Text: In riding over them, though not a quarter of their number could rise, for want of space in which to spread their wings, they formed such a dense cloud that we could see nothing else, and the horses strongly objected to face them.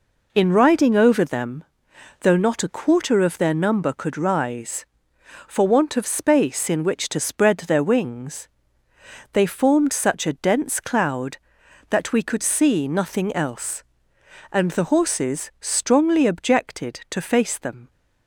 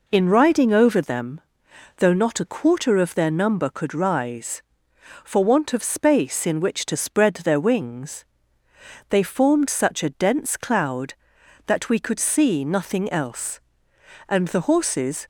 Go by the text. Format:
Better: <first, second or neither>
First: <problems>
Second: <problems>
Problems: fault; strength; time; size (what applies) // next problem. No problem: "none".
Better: first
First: none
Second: stops before "strongly objected to face them"; at 15.2 s